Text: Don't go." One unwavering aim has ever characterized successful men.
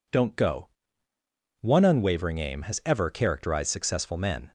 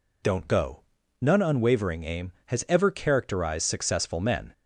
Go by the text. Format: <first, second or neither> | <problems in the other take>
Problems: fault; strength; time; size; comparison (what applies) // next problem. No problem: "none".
first | says "None" for "One"; at 1.2 s